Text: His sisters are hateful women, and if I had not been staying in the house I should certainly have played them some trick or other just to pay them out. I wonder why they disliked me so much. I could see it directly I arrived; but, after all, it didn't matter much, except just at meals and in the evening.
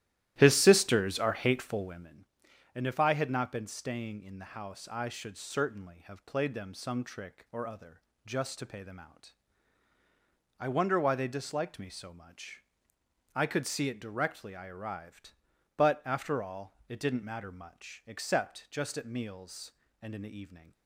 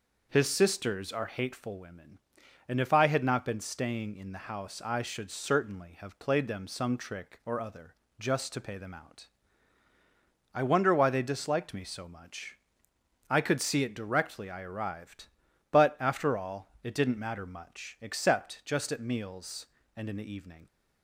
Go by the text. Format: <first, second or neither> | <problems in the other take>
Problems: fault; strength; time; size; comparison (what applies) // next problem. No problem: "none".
second | starts louder than the rest; strong; until 2.3 s; 14 dB // pauses between "other" and "just"; slight; at 8.0 s; 0.26 s long; slight in the second